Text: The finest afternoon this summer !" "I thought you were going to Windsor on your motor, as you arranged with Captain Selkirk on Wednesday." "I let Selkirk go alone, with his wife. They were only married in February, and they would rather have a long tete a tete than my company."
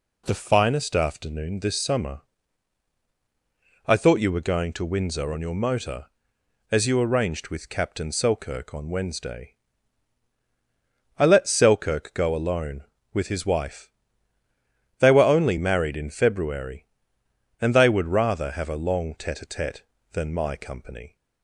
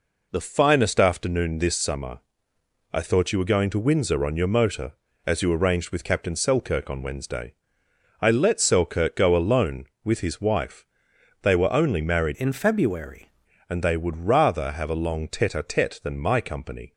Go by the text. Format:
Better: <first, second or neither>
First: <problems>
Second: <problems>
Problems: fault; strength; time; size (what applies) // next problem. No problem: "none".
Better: first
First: none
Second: changes voice from "in" to "February"; from 12.3 to 13.3 s; 1.0 s long